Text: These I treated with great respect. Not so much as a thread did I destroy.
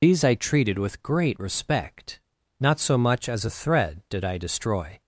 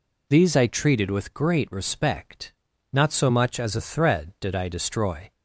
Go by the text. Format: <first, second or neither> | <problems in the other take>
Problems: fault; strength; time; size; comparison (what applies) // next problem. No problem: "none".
second | loses the start of "These"; at 0.0 s; 45 ms